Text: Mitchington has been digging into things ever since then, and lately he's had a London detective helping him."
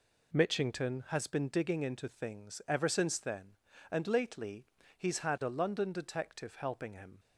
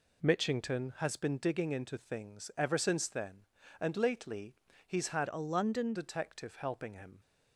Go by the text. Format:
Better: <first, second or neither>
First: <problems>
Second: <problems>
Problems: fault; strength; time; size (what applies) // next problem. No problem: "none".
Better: first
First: pauses between "lately" and "he's"; slight; at 4.6 s; 0.32 s long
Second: pauses between "lately" and "he's"; slight; at 4.5 s; 0.32 s long // changes voice from "a" to "London"; from 5.2 to 5.9 s; 0.7 s long